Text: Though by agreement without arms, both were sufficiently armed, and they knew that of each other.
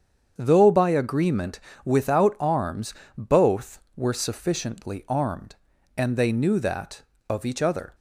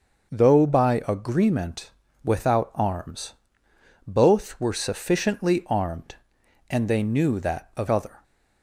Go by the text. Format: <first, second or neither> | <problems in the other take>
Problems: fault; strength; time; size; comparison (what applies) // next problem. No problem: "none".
first | starts louder than the rest; until 1.3 s; 6.5 dB; strong in the first // pauses between "agreement" and "without"; slight; at 1.9 s; 0.32 s long; slight in the first // skips "each"; at 7.8 s